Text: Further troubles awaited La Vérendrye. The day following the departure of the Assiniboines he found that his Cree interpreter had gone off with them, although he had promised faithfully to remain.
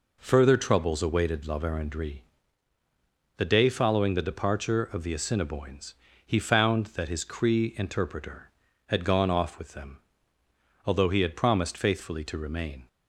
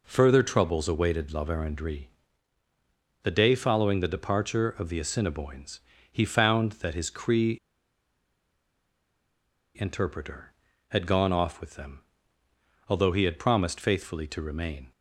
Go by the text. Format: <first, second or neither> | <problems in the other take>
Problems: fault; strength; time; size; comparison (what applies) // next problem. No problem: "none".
first | pauses between "Assiniboines" and "he"; slight; at 5.7 s; 0.32 s long; slight in the first // pauses between "Cree" and "interpreter"; strong; at 7.5 s; 2.2 s long